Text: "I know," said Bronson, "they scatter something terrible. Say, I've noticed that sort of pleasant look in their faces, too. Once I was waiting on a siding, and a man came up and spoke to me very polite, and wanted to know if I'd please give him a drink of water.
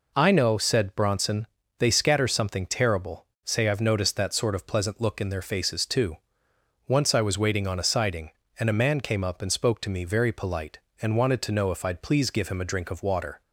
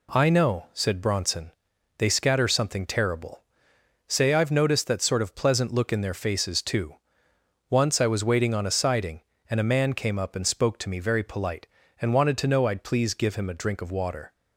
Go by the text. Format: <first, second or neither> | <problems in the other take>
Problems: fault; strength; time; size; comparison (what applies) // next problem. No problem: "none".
first | skips "if"; at 12.6 s